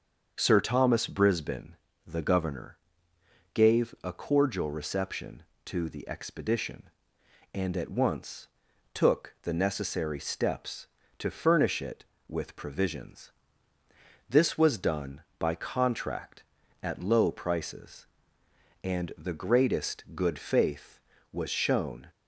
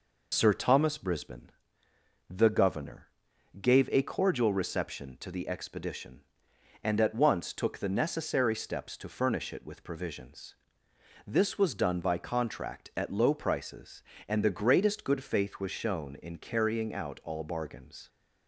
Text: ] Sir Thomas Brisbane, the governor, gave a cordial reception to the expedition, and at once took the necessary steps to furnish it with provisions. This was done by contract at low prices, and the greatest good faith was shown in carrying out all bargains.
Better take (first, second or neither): second